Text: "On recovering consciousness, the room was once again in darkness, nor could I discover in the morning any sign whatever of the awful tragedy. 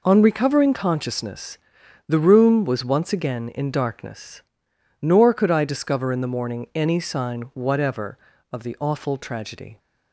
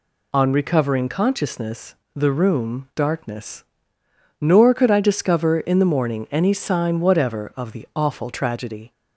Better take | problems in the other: first | skips "was once again in"; at 2.9 s

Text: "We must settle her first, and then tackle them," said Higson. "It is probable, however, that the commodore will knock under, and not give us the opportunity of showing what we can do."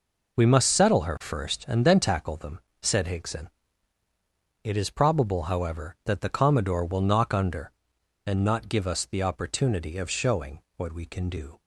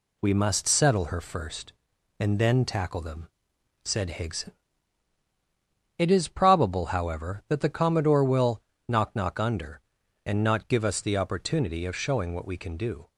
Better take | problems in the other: first | pauses between "will" and "knock"; slight; at 8.6 s; 0.28 s long // says "knock" twice; at 9.1 s

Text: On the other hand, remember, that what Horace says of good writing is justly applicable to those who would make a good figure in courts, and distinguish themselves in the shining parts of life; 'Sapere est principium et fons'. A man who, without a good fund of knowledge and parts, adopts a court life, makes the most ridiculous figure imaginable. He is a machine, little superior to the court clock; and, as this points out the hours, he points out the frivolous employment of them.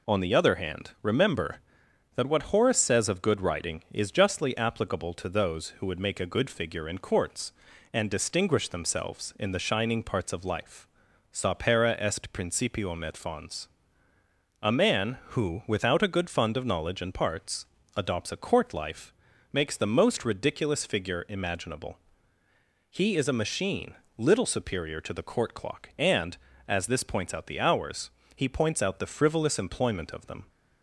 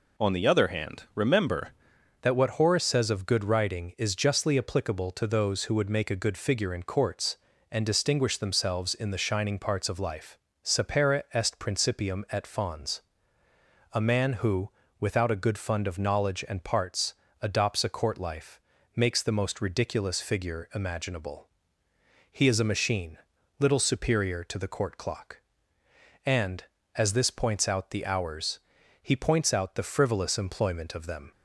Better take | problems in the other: first | changes voice at "that"; from 2.2 s on; 29.1 s long

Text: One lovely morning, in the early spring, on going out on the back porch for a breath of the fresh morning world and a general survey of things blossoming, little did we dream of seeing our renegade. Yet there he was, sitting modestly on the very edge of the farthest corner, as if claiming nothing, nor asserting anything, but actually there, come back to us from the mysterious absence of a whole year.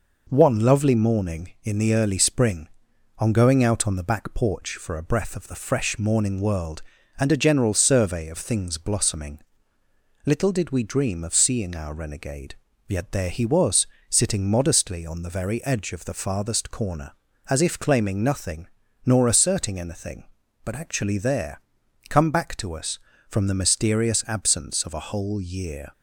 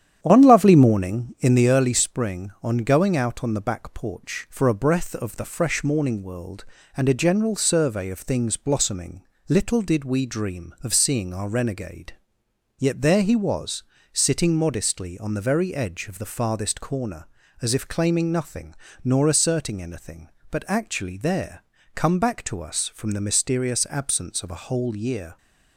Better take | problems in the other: first | starts louder than the rest; strong; until 1.7 s; 9.5 dB

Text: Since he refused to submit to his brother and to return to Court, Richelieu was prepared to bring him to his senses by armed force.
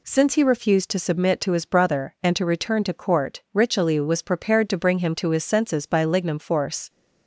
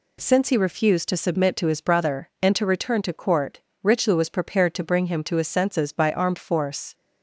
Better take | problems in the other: second | says "lignum" for "armed"; at 6.0 s

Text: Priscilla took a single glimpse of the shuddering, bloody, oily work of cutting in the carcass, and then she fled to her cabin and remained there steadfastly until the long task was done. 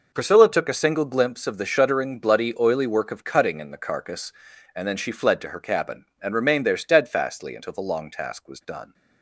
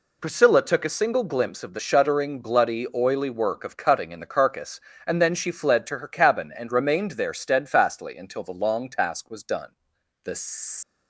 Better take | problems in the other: first | goes on to say "The"; from 10.2 s on; 0.52 s long

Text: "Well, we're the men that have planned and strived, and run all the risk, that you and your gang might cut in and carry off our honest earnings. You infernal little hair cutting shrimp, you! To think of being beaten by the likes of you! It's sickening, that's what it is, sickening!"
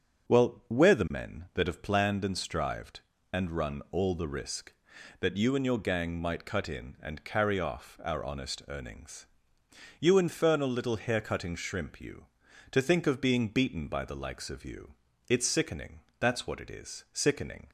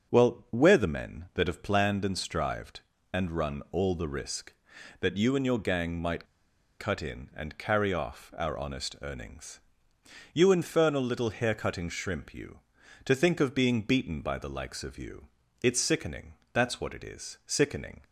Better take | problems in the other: first | starts louder than the rest; until 1.1 s; 6.5 dB; also in the first // pauses between "might" and "cut"; noticeable; at 6.2 s; 0.53 s long

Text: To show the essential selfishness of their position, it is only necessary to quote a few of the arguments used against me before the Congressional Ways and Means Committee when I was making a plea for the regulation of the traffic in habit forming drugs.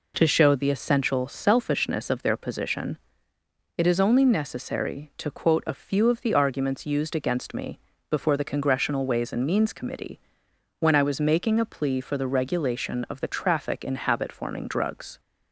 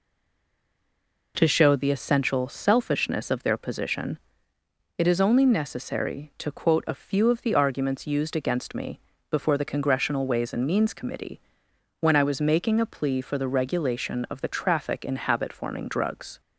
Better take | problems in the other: first | stays silent before the first word; noticeable; until 1.3 s; 1.3 s long // pauses between "me" and "before"; slight; at 8.9 s; 0.30 s long; slight in the first // pauses between "Committee" and "when"; noticeable; at 11.4 s; 0.58 s long; noticeable in the first

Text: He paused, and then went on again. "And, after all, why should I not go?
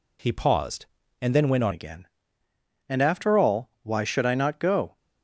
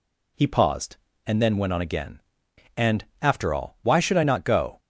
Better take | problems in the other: second | changes voice at "again"; from 1.7 s on; 3.2 s long

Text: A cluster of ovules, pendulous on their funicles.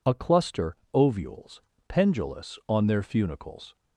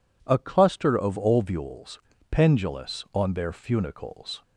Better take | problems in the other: second | skips "of"; at 0.8 s

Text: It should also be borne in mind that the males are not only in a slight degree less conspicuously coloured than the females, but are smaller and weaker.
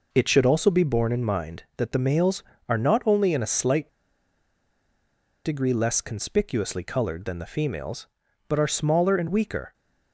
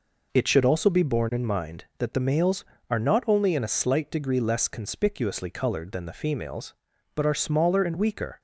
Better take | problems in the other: second | pauses between "slight" and "degree"; strong; at 3.8 s; 1.5 s long

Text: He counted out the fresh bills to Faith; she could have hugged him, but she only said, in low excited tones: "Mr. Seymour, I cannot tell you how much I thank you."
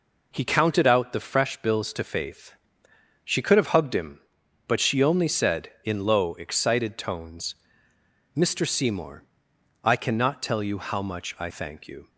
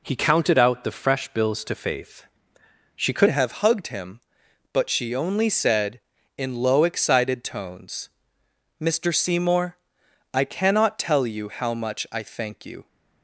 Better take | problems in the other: first | changes voice at "have"; from 3.2 s on; 9.6 s long

